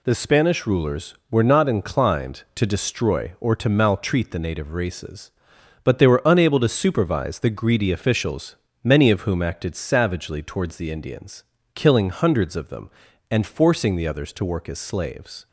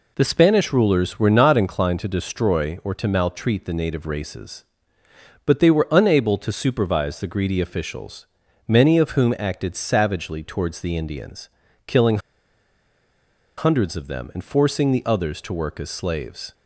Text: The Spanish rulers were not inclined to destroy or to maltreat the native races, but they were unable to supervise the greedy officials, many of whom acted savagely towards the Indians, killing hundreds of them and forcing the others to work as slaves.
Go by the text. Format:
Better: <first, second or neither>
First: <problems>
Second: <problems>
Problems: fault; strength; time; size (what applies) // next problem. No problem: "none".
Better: first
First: none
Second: pauses between "killing" and "hundreds"; strong; at 12.1 s; 1.3 s long